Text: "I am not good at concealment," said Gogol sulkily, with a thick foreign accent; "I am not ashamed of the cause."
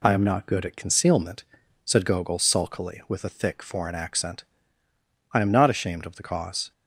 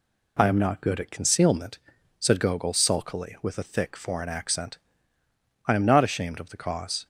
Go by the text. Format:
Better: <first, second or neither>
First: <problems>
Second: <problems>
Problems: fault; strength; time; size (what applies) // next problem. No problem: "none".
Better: neither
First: none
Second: none